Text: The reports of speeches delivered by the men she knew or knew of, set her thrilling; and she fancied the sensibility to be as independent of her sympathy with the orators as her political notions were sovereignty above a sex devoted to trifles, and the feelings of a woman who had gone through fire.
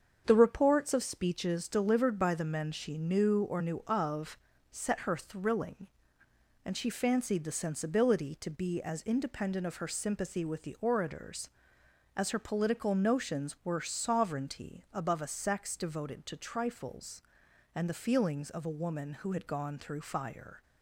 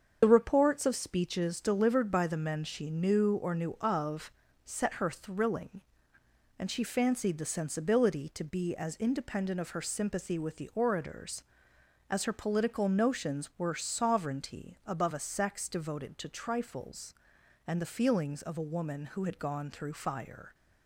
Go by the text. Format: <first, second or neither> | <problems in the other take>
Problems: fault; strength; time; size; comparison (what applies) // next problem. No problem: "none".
first | loses the start of "The"; at 0.2 s; 50 ms // starts louder than the rest; strong; until 1.2 s; 7 dB; strong in the first